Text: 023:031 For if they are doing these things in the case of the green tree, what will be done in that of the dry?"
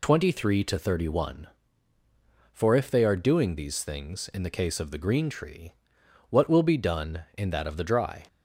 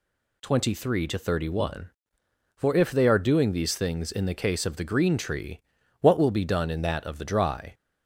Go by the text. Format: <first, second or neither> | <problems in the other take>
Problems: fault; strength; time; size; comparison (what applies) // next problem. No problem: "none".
neither | none